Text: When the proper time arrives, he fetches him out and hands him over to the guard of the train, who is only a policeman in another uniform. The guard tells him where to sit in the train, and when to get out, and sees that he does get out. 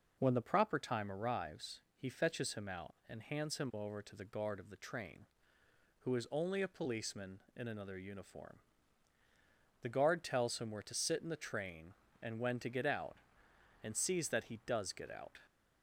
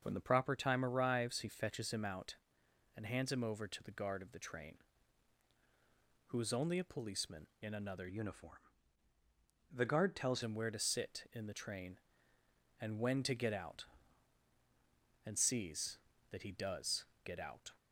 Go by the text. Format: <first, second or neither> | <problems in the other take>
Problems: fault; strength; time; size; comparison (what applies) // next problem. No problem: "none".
first | starts louder than the rest; until 1.0 s; 6.5 dB // changes voice from "uniform" to "tells"; from 8.0 to 10.4 s; 2.4 s long // pauses between "does" and "get"; slight; at 17.0 s; 0.20 s long